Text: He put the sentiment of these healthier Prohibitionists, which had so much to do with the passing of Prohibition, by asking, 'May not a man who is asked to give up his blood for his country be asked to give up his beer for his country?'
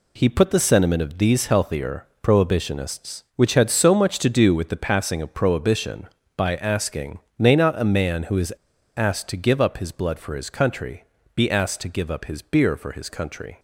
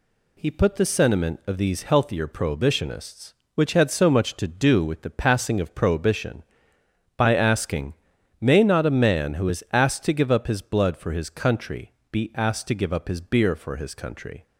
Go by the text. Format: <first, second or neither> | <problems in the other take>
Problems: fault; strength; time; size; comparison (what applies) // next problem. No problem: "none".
second | pauses between "healthier" and "Prohibitionists"; slight; at 2.0 s; 0.16 s long // pauses between "is" and "asked"; noticeable; at 8.5 s; 0.46 s long // pauses between "country" and "be"; slight; at 11.0 s; 0.32 s long; slight in the second